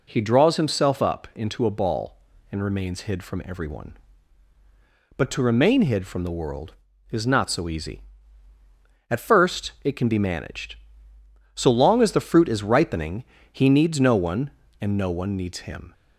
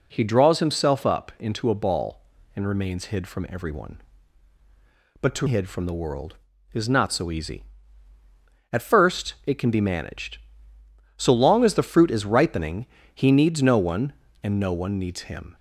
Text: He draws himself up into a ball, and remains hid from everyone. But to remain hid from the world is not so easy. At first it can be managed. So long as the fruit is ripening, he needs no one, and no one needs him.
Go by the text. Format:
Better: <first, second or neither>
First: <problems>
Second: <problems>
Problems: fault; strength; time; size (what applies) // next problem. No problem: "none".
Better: first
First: none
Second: skips "remain"; at 5.4 s